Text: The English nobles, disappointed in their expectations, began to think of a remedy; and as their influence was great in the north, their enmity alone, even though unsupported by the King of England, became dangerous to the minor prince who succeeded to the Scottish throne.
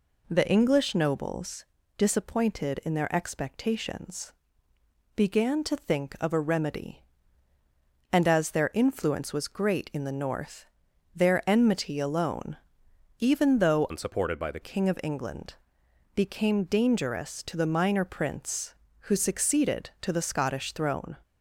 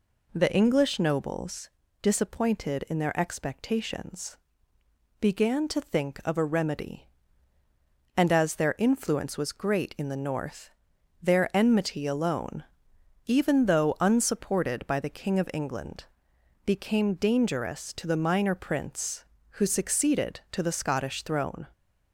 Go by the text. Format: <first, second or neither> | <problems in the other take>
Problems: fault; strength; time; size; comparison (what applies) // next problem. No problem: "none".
second | changes voice from "unsupported" to "the"; from 13.8 to 14.6 s; 0.8 s long